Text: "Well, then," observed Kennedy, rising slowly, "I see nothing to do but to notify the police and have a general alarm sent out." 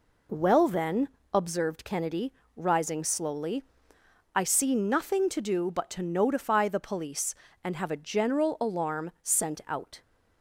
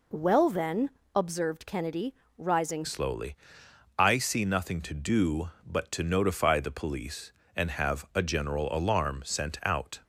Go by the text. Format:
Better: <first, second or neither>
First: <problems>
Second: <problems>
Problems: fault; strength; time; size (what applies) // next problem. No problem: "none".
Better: first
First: none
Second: changes voice at "slowly"; from 2.8 s on; 7.1 s long